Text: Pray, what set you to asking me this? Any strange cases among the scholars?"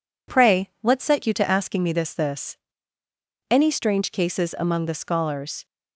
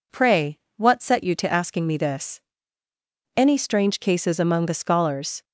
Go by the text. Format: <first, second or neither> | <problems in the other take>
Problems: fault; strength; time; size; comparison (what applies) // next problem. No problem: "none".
second | says "this" twice; at 2.1 s